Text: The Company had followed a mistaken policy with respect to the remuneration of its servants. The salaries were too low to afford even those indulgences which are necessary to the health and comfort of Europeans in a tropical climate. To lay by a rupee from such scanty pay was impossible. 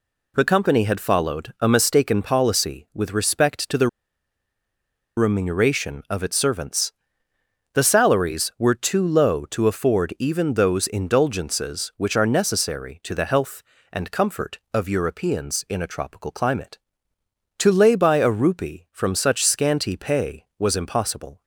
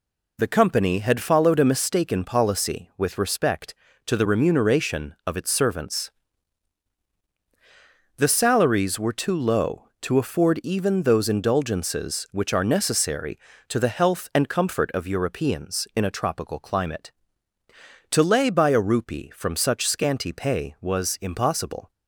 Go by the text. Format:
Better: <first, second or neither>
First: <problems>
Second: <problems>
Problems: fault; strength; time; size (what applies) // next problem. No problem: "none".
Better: second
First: pauses between "the" and "remuneration"; strong; at 3.8 s; 1.3 s long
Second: none